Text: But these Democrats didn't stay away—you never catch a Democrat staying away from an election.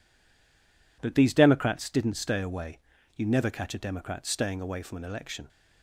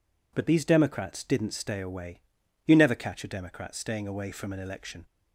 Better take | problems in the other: second | stays silent before the first word; until 1.0 s; 1.0 s long

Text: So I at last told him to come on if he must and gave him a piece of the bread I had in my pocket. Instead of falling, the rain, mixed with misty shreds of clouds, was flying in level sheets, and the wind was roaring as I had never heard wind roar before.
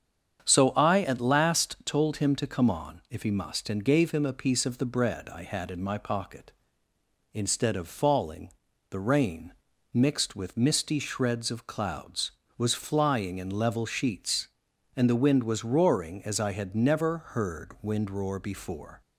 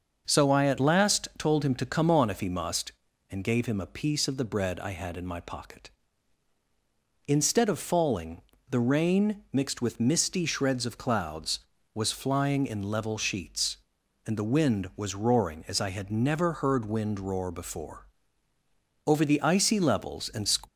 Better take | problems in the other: first | starts louder than the rest; until 1.2 s; 6.5 dB; strong in the first // goes on to say "Over the icy levels and"; from 19.0 s on; 1.4 s long

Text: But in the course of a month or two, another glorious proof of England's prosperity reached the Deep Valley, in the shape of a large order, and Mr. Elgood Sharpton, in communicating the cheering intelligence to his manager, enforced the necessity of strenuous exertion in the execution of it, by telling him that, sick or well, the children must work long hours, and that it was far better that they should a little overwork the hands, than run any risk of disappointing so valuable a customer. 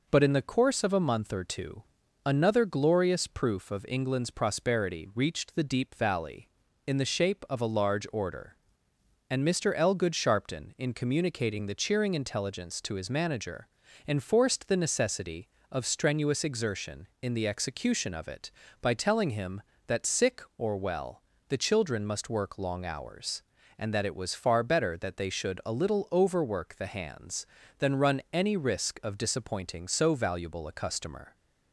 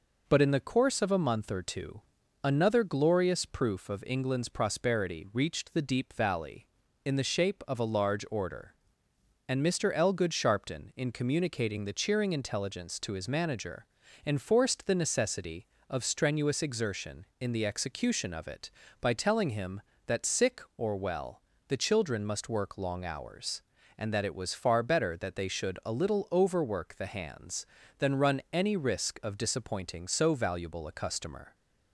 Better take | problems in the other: neither | none

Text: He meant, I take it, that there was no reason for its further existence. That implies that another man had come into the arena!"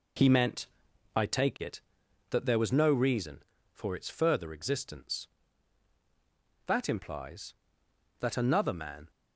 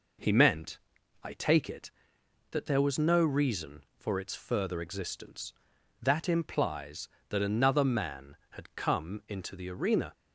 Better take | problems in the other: second | stops before "had come into the arena"; at 9.0 s

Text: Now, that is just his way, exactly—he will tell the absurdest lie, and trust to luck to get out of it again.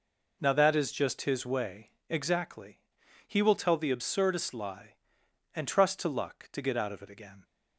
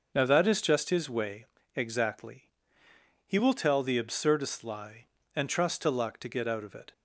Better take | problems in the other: first | stops before "again"; at 6.9 s

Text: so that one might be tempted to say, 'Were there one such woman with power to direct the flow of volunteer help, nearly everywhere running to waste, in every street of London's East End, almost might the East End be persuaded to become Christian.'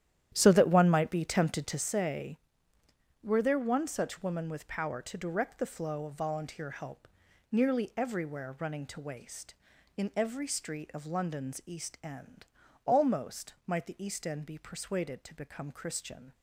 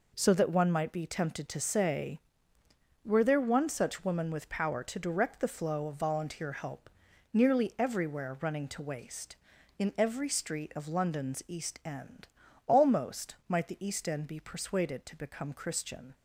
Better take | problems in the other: second | starts louder than the rest; strong; until 1.9 s; 11 dB

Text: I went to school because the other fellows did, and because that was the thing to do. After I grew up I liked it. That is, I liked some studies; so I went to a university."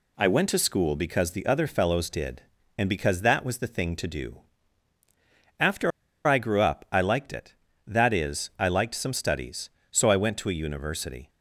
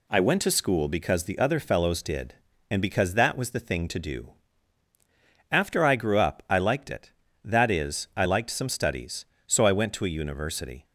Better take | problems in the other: second | pauses between "After" and "I"; at 5.9 s; 0.36 s long

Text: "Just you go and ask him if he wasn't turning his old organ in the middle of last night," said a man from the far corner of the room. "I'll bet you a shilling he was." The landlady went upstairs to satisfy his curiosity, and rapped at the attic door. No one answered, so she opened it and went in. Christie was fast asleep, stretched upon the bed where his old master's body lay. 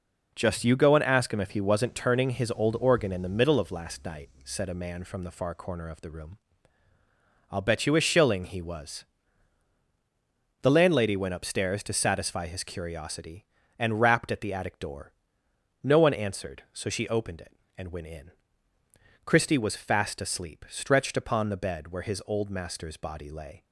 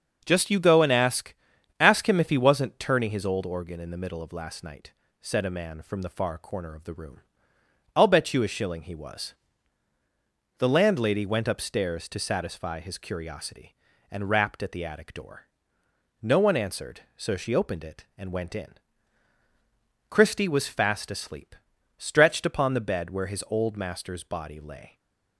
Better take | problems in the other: first | starts louder than the rest; until 1.2 s; 6.5 dB // says "ask" twice; at 1.8 s // stays silent after the last word; slight; from 24.8 s on; 0.5 s long

